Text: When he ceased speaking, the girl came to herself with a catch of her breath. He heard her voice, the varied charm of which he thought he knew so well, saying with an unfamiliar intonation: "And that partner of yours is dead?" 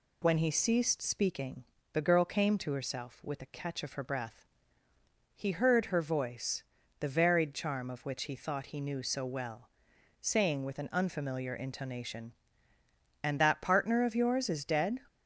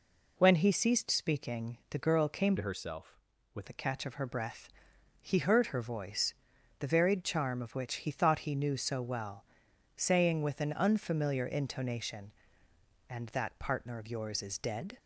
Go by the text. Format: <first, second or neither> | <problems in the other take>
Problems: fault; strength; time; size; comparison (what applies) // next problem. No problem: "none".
first | changes voice from "to" to "with"; from 2.5 to 3.6 s; 1.1 s long